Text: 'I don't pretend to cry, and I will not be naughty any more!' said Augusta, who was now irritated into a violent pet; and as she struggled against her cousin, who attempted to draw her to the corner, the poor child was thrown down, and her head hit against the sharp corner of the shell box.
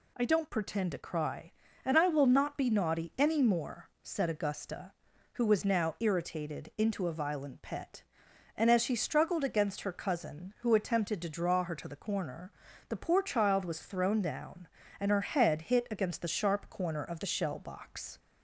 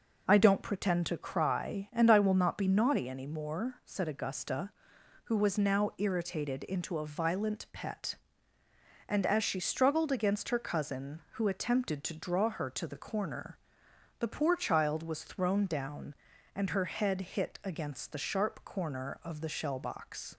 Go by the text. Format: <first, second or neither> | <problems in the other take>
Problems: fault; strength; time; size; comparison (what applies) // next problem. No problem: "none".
neither | none